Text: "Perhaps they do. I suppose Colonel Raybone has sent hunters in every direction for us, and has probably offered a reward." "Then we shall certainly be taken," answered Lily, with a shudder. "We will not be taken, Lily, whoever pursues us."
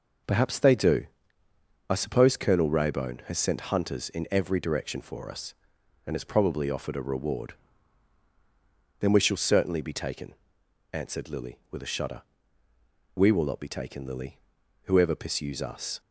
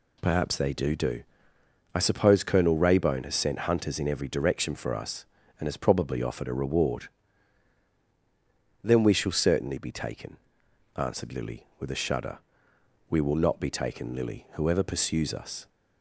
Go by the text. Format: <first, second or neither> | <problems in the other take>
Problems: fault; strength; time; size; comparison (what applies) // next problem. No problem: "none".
first | says "do" twice; at 0.9 s